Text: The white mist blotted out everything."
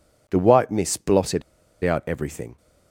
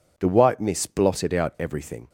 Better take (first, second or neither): second